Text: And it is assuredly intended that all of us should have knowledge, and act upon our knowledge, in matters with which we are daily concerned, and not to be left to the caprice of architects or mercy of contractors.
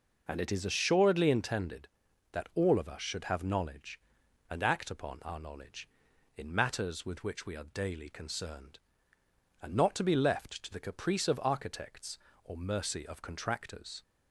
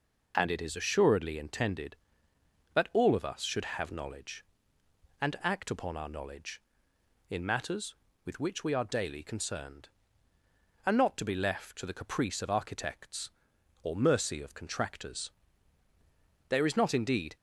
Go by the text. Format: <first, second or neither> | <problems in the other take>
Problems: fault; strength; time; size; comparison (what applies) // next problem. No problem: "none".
first | goes on to say "There is not indeed"; noticeable; from 16.4 s on; 0.88 s long